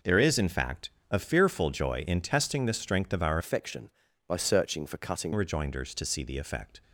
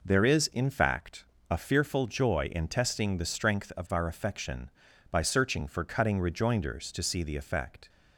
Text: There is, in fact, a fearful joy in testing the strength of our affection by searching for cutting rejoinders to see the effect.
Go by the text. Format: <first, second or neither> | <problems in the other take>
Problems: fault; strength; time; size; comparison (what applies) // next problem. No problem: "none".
second | changes voice from "affection" to "cutting"; from 3.3 to 5.3 s; 2.0 s long